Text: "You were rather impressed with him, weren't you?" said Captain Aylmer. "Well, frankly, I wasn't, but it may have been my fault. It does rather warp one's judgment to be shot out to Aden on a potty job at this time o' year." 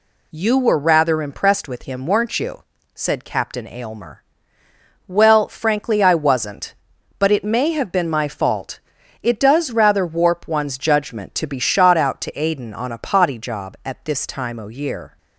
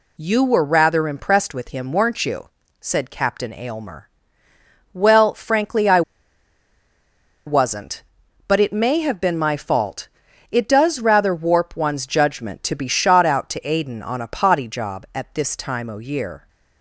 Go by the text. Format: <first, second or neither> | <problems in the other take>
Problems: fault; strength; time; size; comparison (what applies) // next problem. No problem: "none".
first | pauses between "I" and "wasn't"; strong; at 6.0 s; 1.4 s long